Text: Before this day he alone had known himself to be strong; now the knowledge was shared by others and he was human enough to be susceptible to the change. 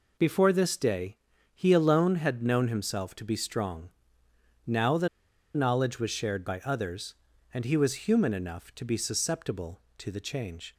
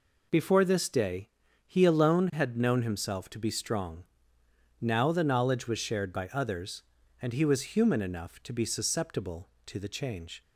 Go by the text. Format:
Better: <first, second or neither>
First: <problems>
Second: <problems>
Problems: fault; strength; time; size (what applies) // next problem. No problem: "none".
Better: second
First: pauses between "day" and "he"; slight; at 1.1 s; 0.36 s long // pauses between "the" and "knowledge"; noticeable; at 5.0 s; 0.49 s long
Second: pauses between "day" and "he"; slight; at 1.2 s; 0.36 s long